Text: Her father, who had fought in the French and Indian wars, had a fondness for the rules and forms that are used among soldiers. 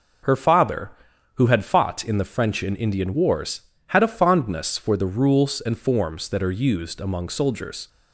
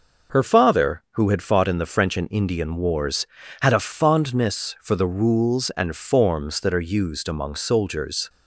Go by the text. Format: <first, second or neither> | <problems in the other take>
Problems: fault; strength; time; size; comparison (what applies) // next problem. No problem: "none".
first | changes voice at "father"; from 0.4 s on; 7.8 s long